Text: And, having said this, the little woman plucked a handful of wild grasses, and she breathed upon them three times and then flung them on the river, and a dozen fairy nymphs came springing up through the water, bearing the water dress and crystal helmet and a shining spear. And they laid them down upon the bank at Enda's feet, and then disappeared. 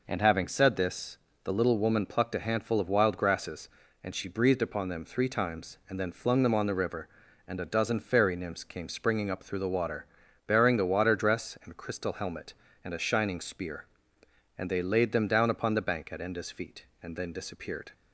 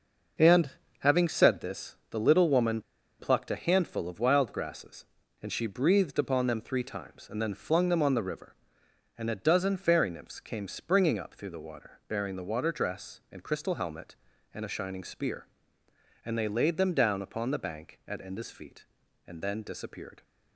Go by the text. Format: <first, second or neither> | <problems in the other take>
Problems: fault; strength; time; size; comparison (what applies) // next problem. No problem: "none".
first | pauses between "woman" and "plucked"; at 2.7 s; 0.39 s long